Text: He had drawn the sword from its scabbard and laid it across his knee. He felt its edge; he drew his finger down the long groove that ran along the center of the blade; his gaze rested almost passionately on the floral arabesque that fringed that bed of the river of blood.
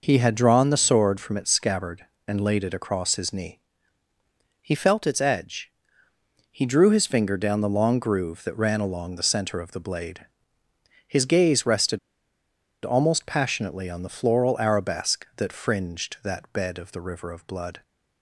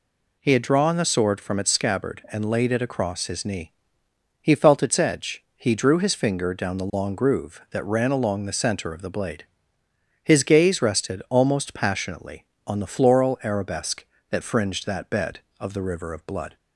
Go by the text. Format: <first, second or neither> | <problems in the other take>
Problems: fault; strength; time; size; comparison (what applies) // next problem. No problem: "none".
second | pauses between "rested" and "almost"; noticeable; at 11.9 s; 0.87 s long